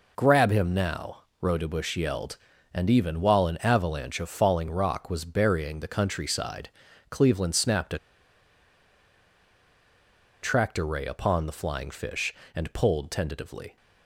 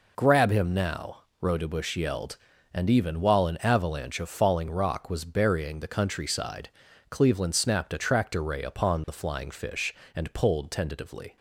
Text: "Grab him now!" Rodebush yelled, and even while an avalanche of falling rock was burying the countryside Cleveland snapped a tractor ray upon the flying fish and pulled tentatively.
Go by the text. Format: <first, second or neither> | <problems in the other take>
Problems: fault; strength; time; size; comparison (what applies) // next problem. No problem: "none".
second | pauses between "countryside" and "Cleveland"; at 6.6 s; 0.42 s long; also in the second // pauses between "a" and "tractor"; strong; at 7.9 s; 2.4 s long